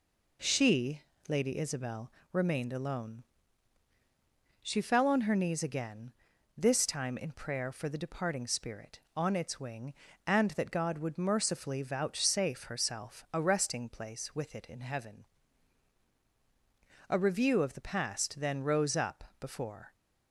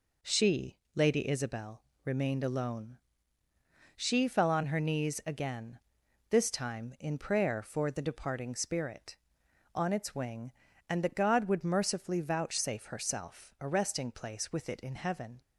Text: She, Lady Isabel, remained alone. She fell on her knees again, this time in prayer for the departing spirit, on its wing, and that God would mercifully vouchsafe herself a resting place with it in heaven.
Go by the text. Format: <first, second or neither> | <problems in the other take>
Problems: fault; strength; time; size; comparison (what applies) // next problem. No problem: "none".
second | goes on to say "A review of the past then rose up before"; strong; from 17.1 s on; 2.8 s long